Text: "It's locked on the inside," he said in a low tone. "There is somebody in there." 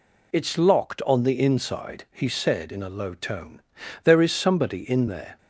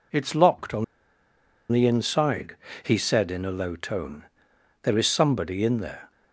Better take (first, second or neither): first